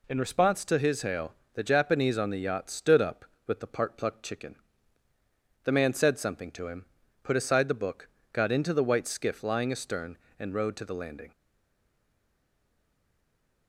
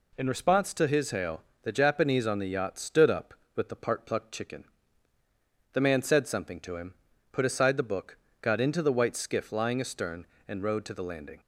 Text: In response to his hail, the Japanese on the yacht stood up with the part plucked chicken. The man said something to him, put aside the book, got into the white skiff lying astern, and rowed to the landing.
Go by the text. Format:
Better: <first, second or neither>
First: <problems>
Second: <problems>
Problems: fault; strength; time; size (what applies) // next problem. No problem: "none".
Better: second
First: stays silent after the last word; from 11.3 s on; 2.3 s long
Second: none